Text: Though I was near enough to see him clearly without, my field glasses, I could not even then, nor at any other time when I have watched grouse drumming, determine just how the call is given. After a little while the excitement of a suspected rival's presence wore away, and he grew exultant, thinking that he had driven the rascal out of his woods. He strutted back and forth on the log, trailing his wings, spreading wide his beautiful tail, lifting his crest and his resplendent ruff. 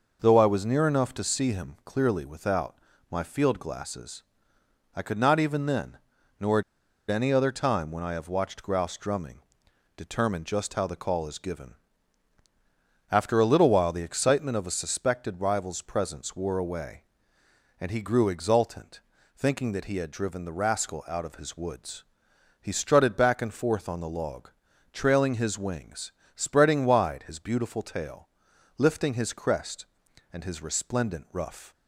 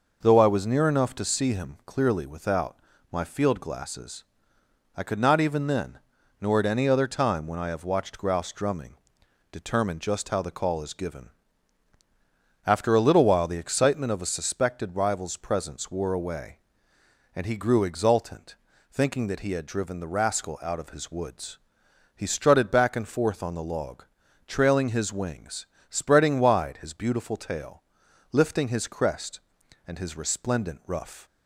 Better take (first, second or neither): second